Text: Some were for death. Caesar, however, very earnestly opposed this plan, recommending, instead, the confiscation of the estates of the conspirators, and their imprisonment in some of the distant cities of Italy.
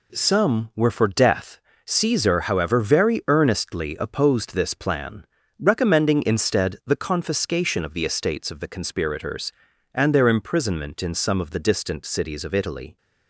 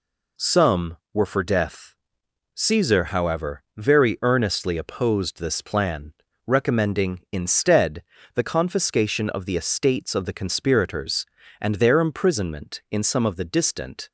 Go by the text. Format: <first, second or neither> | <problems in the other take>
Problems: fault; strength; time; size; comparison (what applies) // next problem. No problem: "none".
first | stops before "cities of Italy"; at 14.0 s